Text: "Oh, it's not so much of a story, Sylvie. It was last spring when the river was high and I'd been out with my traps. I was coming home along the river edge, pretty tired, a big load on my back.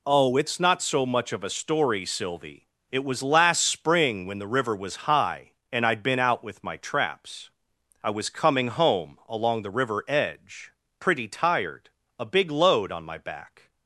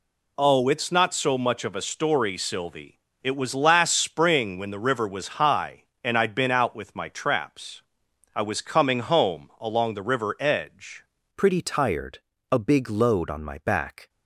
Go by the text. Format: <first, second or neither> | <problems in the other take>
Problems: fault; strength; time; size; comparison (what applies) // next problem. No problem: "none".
first | changes voice at "pretty"; from 11.3 s on; 2.7 s long